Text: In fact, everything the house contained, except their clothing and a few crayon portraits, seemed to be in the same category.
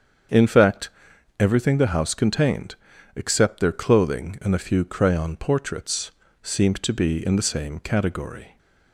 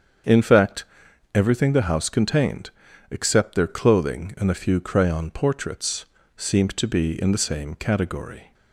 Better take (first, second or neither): neither